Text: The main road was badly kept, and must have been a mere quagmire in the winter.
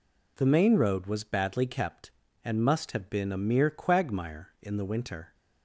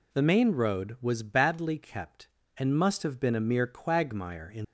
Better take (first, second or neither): first